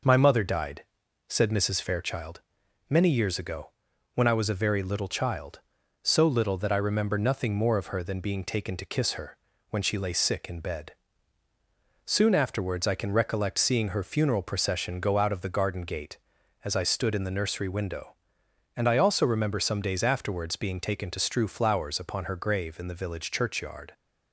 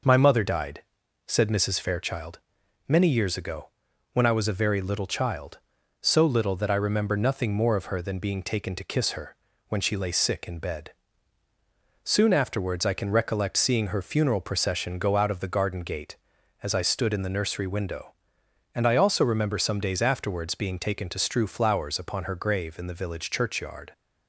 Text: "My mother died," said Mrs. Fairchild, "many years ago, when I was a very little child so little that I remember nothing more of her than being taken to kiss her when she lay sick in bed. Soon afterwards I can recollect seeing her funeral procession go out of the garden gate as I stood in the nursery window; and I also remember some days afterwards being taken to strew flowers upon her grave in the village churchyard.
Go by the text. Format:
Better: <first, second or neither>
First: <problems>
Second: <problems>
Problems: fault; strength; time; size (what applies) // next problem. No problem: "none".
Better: neither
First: pauses between "her" and "when"; slight; at 9.3 s; 0.32 s long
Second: pauses between "her" and "when"; slight; at 9.3 s; 0.32 s long